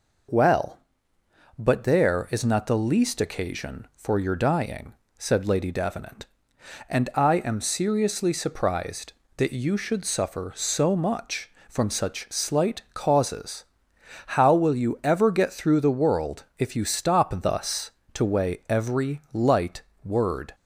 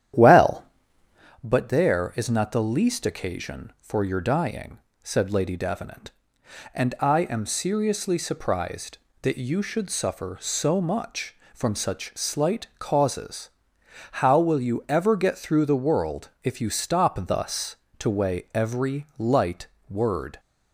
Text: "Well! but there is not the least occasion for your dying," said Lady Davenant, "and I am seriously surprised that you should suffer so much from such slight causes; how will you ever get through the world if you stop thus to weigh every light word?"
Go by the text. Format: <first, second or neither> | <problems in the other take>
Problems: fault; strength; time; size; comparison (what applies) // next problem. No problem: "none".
first | starts louder than the rest; strong; until 1.4 s; 10.5 dB // pauses between "world" and "if"; slight; at 16.2 s; 0.16 s long; slight in the first // pauses between "light" and "word"; slight; at 19.6 s; 0.22 s long; slight in the first